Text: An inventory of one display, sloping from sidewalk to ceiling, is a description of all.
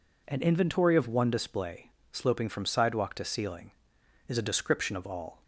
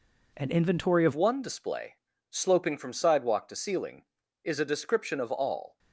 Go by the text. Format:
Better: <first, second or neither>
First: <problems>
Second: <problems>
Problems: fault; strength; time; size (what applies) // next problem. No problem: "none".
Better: first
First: none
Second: changes voice at "one"; from 1.1 s on; 4.6 s long